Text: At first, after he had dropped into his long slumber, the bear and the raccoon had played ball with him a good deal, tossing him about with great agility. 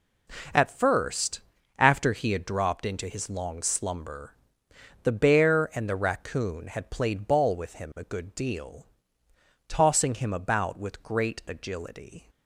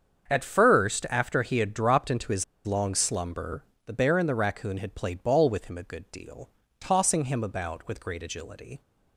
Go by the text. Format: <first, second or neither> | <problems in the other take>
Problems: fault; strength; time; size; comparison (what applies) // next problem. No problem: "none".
first | starts louder than the rest; until 1.3 s; 7 dB // pauses between "his" and "long"; slight; at 2.4 s; 0.20 s long